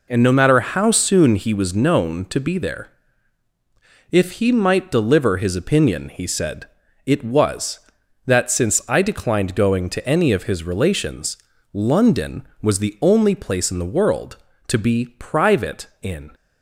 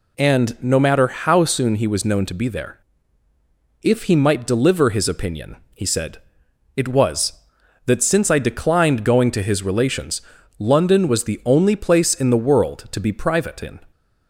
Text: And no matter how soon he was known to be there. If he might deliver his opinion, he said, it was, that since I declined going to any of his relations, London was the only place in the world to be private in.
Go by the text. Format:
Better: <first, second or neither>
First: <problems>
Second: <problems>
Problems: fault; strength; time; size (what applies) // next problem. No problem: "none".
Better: first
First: none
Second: skips "any of"; at 9.4 s